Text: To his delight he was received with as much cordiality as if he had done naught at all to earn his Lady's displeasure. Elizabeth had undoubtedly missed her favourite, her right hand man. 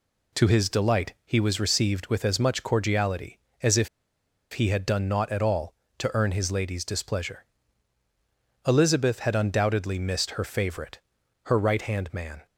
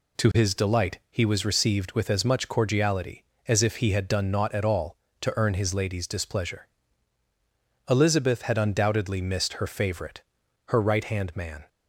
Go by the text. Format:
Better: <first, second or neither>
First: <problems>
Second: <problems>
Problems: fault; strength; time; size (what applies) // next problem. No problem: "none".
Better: second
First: pauses between "if" and "he"; noticeable; at 3.8 s; 0.65 s long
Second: none